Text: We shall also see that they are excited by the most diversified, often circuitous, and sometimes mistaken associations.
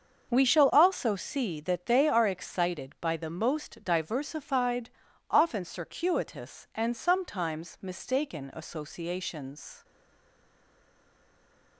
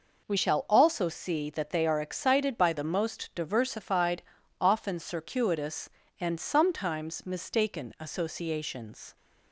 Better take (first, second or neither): second